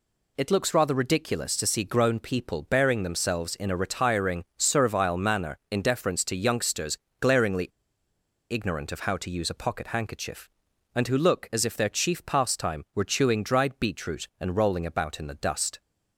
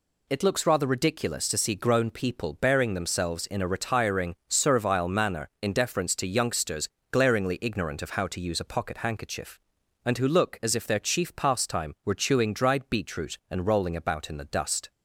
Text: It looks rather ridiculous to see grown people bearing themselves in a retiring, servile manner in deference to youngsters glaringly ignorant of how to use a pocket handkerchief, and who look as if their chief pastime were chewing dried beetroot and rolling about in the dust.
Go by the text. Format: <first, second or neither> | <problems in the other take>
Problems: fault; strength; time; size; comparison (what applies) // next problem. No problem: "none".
second | pauses between "youngsters" and "glaringly"; slight; at 6.9 s; 0.22 s long; slight in the second // pauses between "glaringly" and "ignorant"; noticeable; at 7.6 s; 0.82 s long